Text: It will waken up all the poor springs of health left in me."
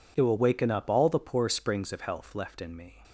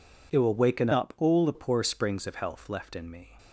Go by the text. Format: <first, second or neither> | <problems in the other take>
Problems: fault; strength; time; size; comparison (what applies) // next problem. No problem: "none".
first | changes voice from "up" to "the"; from 0.9 to 1.5 s; 0.6 s long